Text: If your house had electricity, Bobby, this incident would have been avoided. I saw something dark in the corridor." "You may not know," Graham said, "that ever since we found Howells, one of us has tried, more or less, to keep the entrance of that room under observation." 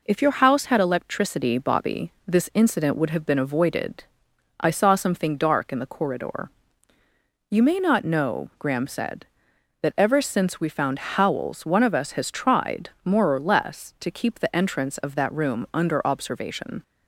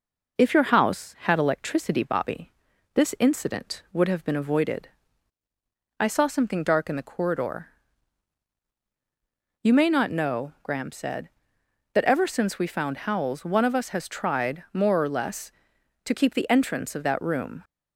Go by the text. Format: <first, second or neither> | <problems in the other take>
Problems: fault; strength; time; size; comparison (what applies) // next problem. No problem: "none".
first | stops before "under observation"; at 17.6 s